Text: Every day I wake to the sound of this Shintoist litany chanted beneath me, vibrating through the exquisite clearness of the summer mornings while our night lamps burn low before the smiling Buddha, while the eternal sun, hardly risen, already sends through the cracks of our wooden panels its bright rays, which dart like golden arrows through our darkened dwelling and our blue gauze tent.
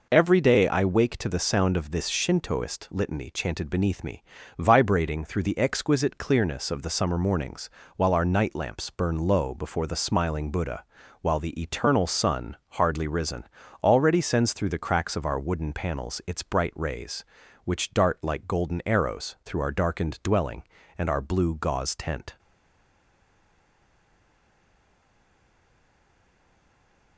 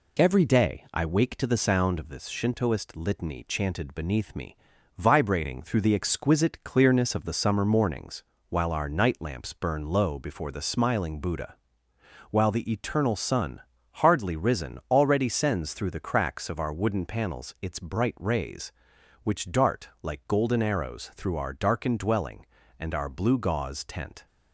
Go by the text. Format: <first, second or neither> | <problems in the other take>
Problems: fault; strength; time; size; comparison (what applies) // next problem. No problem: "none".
second | pauses between "mornings" and "while"; slight; at 7.6 s; 0.30 s long; slight in the second // stays silent after the last word; strong; from 22.3 s on; 4.8 s long